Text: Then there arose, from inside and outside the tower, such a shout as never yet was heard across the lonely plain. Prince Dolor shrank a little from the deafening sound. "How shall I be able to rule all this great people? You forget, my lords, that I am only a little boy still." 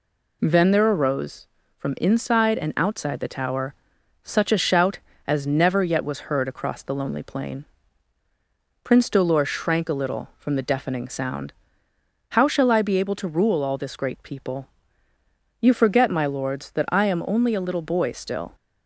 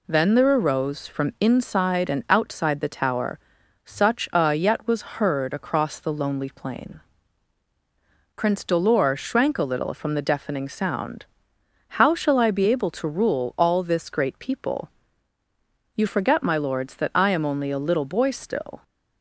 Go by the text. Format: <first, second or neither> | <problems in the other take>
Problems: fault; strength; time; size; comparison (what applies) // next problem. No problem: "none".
first | skips "shout as never"; at 4.5 s